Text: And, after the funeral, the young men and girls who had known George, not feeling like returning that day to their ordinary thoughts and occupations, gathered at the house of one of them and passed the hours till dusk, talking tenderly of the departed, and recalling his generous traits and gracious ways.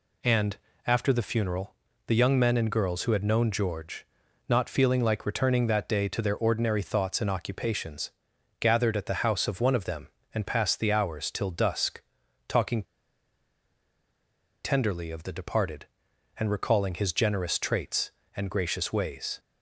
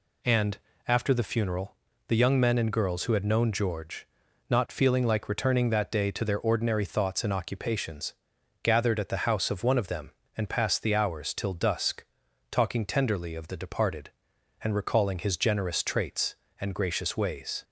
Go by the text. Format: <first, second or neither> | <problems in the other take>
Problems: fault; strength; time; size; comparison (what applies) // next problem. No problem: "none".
second | pauses between "talking" and "tenderly"; strong; at 12.8 s; 1.8 s long